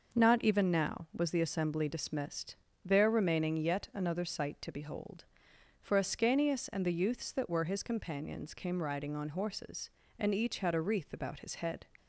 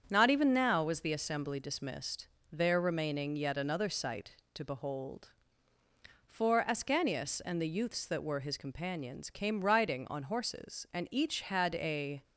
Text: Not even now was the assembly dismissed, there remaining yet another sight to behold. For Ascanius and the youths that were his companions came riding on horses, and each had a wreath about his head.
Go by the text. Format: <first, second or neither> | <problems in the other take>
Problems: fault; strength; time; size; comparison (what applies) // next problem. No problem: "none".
first | starts louder than the rest; strong; until 1.1 s; 7.5 dB // stops before "wreath about his head"; at 12.2 s